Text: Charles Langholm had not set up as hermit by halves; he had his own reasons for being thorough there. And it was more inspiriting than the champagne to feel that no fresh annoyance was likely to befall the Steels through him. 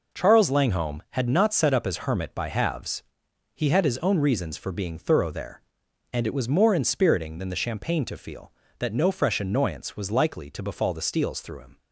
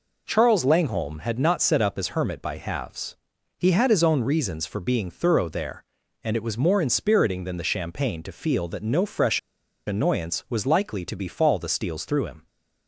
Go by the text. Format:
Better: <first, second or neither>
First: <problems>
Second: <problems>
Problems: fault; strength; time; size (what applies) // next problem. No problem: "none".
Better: first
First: none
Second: pauses between "fresh" and "annoyance"; noticeable; at 9.3 s; 0.47 s long